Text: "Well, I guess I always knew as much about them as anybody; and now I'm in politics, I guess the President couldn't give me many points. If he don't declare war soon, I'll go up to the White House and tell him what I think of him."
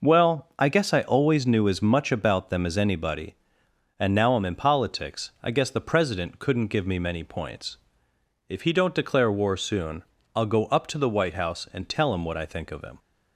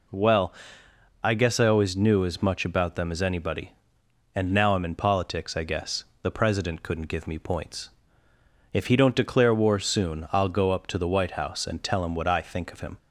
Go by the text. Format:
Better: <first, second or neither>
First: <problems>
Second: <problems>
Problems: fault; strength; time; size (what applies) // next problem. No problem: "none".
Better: first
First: none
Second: pauses between "guess" and "the"; slight; at 6.0 s; 0.18 s long // skips "many"; at 7.3 s